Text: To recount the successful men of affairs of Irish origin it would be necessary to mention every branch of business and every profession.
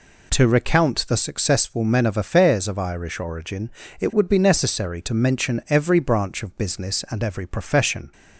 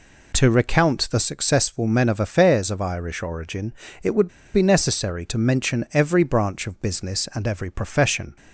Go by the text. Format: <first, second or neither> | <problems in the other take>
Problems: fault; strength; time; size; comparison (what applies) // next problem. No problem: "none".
first | pauses between "origin" and "it"; slight; at 3.7 s; 0.30 s long; slight in the first // pauses between "would" and "be"; slight; at 4.2 s; 0.25 s long